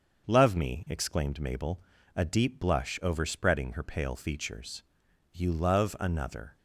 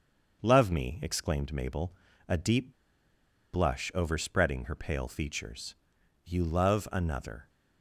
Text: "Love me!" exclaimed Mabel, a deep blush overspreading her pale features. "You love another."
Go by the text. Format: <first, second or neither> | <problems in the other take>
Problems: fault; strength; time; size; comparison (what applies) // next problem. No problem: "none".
first | starts louder than the rest; until 1.4 s; 6.5 dB; also in the first // pauses between "deep" and "blush"; noticeable; at 2.7 s; 0.82 s long